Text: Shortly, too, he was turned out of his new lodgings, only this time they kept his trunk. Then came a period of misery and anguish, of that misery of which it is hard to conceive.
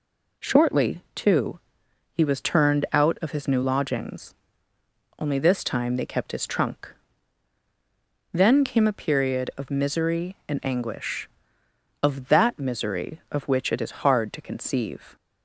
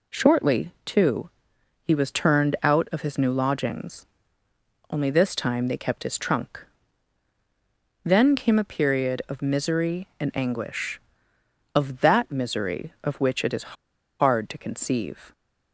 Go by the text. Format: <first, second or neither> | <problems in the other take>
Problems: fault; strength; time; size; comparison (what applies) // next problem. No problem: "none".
first | pauses between "is" and "hard"; noticeable; at 13.7 s; 0.48 s long